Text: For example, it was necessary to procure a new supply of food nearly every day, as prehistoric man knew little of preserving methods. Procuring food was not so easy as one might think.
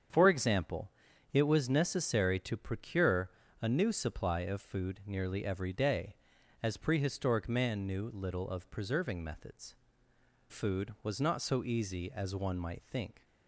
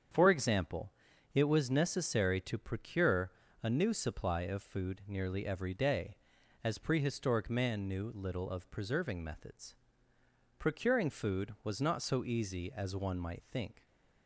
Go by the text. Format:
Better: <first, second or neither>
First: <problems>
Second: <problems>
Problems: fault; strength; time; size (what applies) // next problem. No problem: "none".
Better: second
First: starts louder than the rest; strong; until 1.5 s; 7.5 dB // pauses between "procure" and "a"; slight; at 3.2 s; 0.32 s long // skips "Procuring"; at 10.1 s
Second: starts louder than the rest; strong; until 1.5 s; 7.5 dB // pauses between "procure" and "a"; slight; at 3.3 s; 0.32 s long